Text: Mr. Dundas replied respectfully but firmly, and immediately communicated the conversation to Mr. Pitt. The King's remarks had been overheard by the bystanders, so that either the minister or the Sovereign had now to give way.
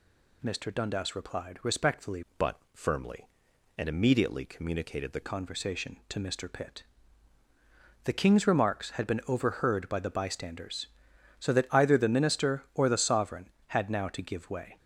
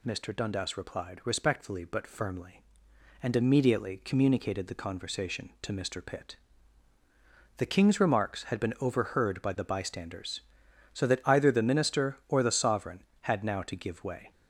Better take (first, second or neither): second